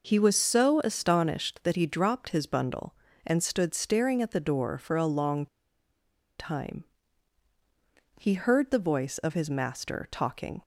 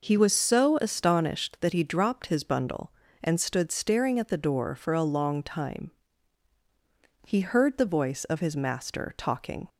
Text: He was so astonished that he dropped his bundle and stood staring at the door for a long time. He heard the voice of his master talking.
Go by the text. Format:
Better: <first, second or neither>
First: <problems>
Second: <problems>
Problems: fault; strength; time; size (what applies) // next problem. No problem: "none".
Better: second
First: pauses between "long" and "time"; noticeable; at 5.4 s; 0.93 s long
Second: none